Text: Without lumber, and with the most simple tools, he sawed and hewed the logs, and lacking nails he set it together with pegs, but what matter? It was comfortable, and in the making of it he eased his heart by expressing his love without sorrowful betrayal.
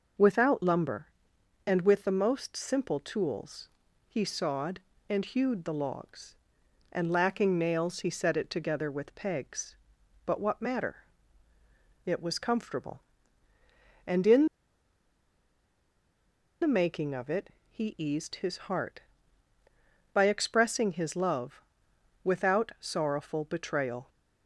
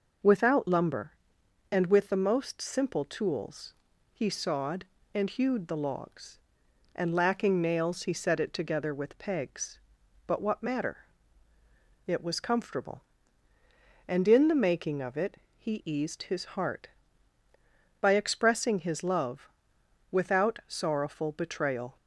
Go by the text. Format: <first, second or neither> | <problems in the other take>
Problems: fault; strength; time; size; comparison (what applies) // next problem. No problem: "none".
second | pauses between "in" and "the"; strong; at 14.4 s; 2.1 s long // pauses between "it" and "he"; slight; at 17.4 s; 0.22 s long; slight in the second // pauses between "love" and "without"; noticeable; at 21.6 s; 0.64 s long; noticeable in the second